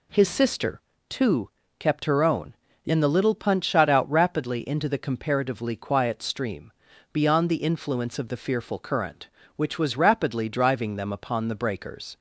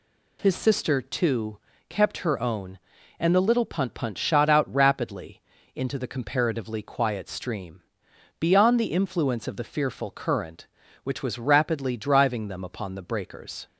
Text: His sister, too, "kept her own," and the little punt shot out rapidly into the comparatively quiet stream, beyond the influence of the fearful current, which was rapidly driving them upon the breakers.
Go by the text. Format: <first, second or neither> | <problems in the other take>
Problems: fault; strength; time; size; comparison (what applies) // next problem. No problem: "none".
first | says "punt" twice; at 3.9 s // pauses between "rapidly" and "into"; slight; at 5.4 s; 0.32 s long